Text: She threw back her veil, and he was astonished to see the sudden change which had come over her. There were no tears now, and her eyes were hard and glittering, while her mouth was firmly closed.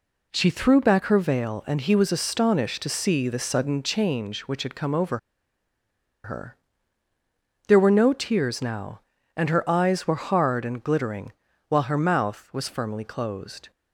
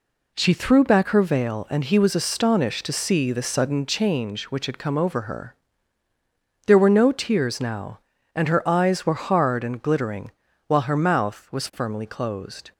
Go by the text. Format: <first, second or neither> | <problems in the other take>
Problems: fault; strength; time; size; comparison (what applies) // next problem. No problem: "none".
second | pauses between "over" and "her"; at 5.1 s; 1.0 s long